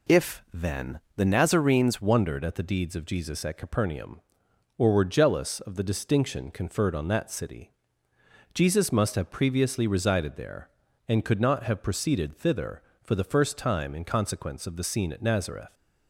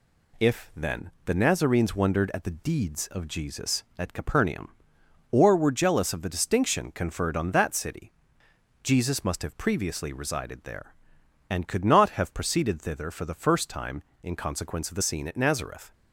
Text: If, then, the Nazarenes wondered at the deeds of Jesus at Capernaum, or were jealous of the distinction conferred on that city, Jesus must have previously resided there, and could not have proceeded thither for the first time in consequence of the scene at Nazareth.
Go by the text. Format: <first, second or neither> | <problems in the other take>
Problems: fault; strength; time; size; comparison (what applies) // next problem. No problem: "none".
second | changes voice at "wondered"; from 2.0 s on; 13.7 s long